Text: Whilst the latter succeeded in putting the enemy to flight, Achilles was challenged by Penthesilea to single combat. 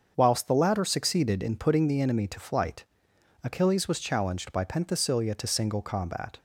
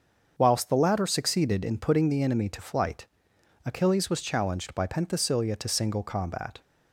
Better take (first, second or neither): neither